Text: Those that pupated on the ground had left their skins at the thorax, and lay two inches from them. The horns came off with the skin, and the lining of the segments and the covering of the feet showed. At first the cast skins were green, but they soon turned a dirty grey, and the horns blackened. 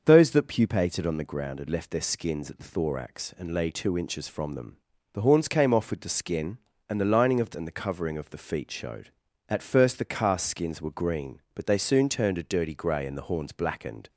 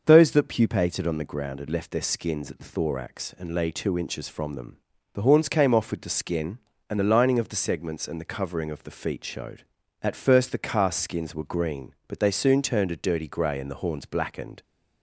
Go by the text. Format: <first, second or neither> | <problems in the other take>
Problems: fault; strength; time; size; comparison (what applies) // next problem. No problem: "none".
second | starts louder than the rest; until 1.0 s; 6.5 dB; also in the second // skips "segments"; at 7.5 s